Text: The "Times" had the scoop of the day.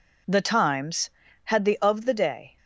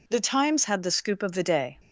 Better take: second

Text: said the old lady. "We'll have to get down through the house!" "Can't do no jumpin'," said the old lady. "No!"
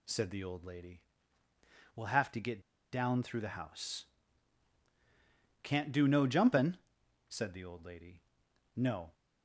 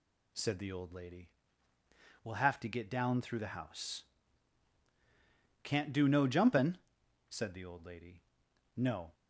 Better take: second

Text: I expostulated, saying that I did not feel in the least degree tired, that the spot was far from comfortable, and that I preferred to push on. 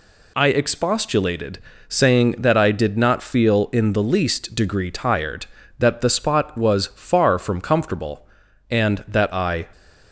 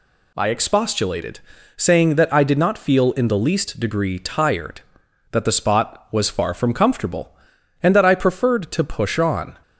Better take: second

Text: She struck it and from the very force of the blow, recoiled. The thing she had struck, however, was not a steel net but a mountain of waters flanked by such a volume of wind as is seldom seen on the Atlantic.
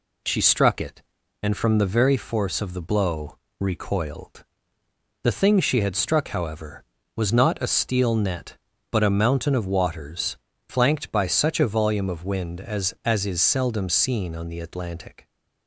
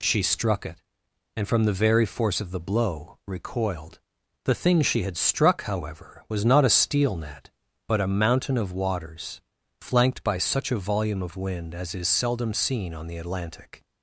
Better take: second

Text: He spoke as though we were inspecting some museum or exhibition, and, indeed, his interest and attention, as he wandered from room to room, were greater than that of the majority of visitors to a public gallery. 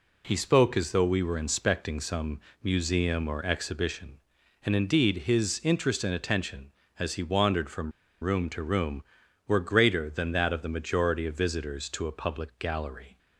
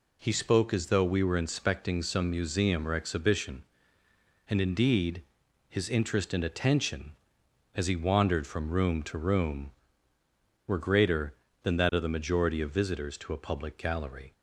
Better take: second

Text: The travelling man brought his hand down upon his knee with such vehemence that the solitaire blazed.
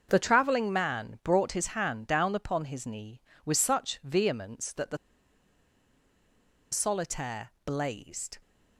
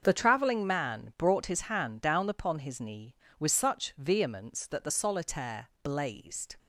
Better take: second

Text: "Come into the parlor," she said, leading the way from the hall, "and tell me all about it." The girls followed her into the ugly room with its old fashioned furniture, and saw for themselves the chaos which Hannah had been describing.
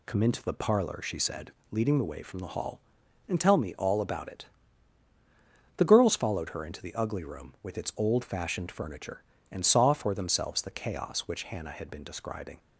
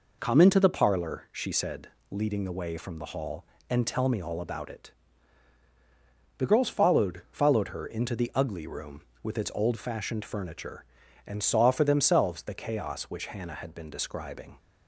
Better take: first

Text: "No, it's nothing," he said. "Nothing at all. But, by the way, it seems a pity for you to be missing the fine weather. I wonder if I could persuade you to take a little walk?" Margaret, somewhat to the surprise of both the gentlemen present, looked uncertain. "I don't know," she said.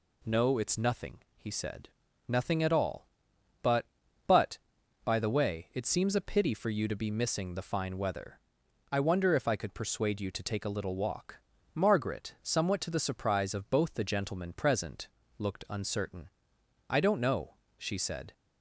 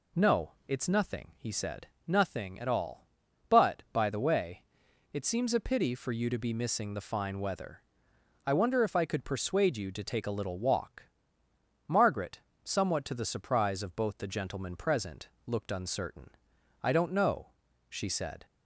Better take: second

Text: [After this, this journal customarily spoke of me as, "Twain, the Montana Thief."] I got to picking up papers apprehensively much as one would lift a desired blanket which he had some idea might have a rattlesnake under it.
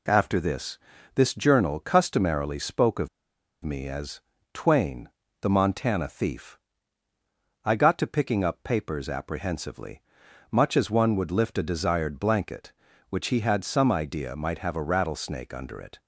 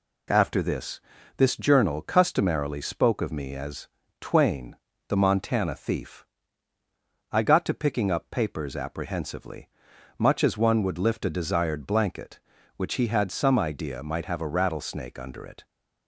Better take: second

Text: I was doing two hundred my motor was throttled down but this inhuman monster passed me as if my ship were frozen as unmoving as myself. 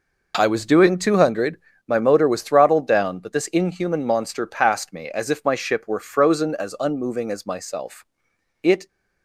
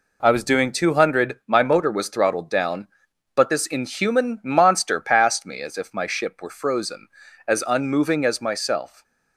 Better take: second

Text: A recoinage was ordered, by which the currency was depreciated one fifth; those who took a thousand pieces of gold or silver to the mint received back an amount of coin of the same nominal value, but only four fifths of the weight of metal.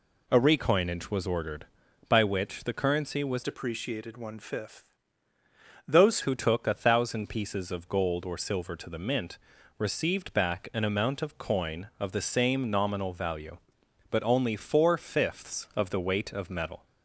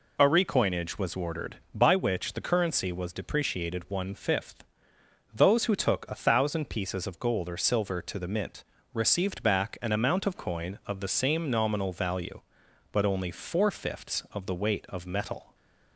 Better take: second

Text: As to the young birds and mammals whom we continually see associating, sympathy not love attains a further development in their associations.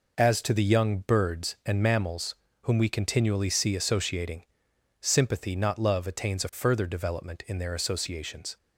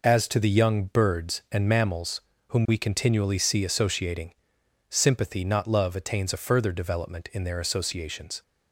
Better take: neither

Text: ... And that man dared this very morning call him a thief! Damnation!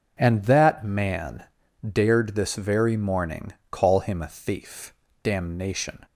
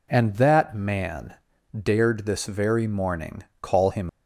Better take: first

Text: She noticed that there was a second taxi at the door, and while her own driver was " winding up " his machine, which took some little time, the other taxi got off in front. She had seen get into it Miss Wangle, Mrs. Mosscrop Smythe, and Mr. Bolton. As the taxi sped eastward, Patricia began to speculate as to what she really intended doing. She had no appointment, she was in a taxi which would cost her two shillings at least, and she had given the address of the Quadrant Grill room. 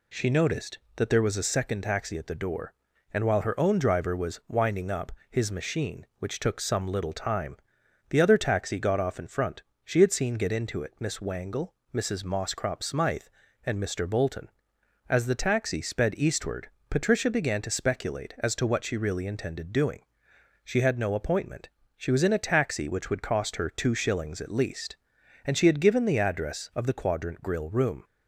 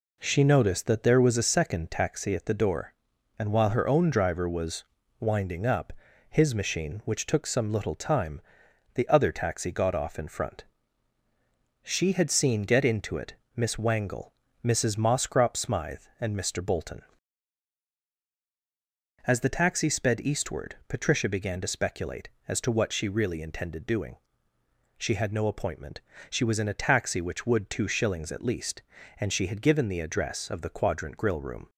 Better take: first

